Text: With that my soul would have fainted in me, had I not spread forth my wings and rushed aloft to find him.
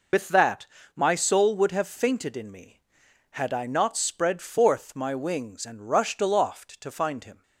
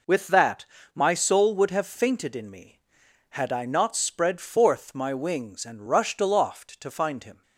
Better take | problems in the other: second | loses the start of "With"; at 0.1 s; 60 ms // pauses between "that" and "my"; slight; at 0.6 s; 0.30 s long; slight in the second

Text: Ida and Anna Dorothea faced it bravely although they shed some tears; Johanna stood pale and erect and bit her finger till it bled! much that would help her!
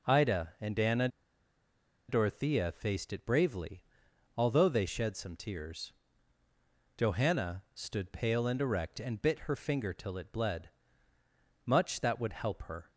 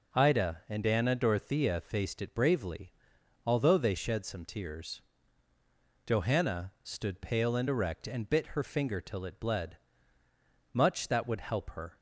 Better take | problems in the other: second | pauses between "Anna" and "Dorothea"; at 1.0 s; 1.0 s long // pauses between "bravely" and "although"; noticeable; at 3.8 s; 0.56 s long; noticeable in the second

